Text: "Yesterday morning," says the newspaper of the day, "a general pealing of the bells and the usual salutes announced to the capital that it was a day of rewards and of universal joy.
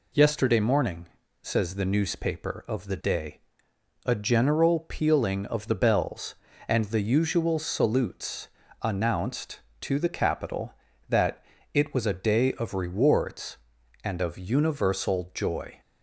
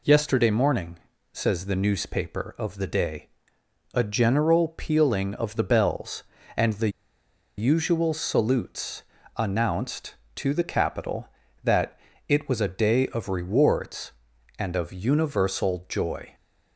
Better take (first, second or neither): first